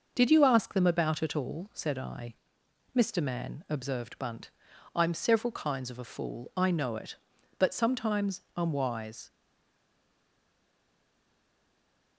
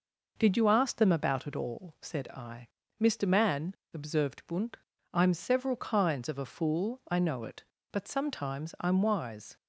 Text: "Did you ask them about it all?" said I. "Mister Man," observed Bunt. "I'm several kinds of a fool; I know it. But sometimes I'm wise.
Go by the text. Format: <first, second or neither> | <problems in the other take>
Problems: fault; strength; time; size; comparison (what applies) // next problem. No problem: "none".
second | stays silent after the last word; strong; from 9.2 s on; 2.9 s long